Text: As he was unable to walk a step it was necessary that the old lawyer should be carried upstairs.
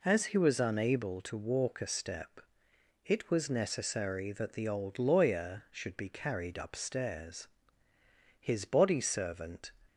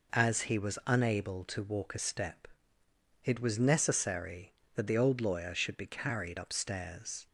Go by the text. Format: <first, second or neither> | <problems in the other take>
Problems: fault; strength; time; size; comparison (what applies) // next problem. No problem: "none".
second | pauses between "step" and "it"; noticeable; at 2.3 s; 0.66 s long; noticeable in the second // goes on to say "His body servant"; from 8.3 s on; 1.3 s long